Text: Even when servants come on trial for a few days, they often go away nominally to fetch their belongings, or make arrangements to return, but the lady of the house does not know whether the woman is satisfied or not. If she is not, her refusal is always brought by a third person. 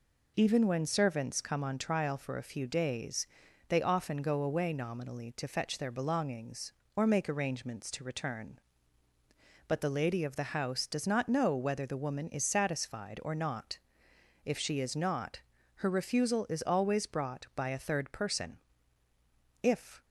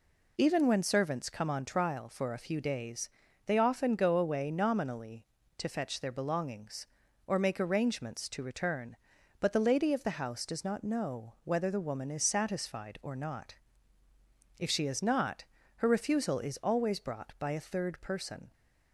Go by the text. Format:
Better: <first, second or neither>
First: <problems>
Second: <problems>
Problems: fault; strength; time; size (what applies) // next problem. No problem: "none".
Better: second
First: goes on to say "If"; slight; from 19.6 s on; 0.42 s long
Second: none